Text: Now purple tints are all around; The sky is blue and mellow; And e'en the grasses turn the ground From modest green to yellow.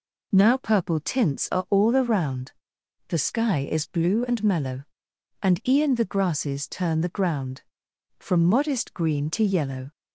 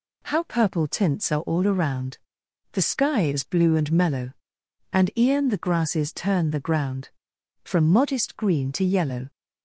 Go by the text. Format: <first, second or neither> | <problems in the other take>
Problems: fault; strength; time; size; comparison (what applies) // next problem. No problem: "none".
first | says "How" for "Now"; at 0.2 s